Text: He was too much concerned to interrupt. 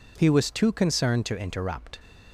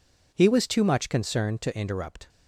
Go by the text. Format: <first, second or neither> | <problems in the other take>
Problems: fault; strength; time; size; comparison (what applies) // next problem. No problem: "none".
second | skips "much"; at 0.7 s